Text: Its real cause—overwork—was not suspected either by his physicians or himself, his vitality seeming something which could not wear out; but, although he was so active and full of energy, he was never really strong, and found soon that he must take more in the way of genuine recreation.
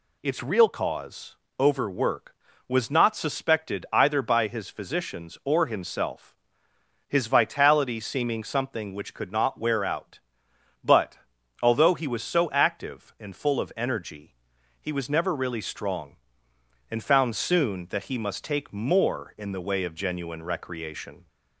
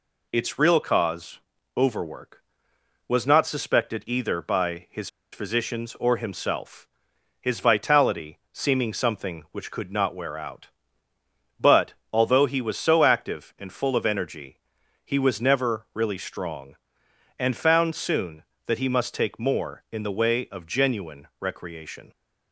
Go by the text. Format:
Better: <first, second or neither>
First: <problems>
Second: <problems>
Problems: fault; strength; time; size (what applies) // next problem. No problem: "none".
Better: first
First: none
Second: pauses between "his" and "physicians"; slight; at 5.0 s; 0.24 s long